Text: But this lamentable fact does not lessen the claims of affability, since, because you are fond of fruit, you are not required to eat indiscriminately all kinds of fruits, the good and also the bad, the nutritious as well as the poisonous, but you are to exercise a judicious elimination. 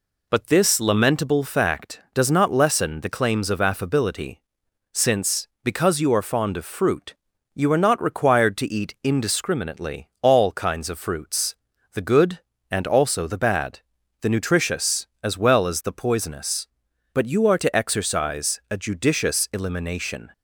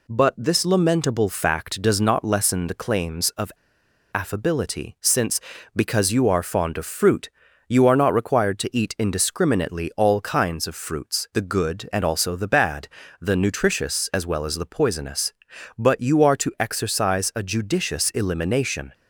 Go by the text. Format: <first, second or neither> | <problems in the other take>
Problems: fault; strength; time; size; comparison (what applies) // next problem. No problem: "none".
first | pauses between "of" and "affability"; noticeable; at 3.5 s; 0.63 s long